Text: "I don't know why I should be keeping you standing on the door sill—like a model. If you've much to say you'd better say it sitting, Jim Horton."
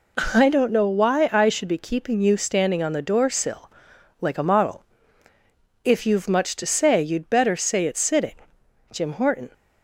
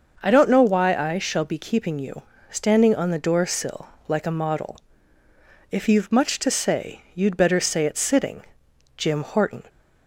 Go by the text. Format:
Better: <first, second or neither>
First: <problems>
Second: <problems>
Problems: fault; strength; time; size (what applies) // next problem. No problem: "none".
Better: first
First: none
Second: starts louder than the rest; noticeable; until 1.2 s; 6 dB // says "shall" for "should"; at 1.1 s // pauses between "you" and "standing"; slight; at 2.2 s; 0.26 s long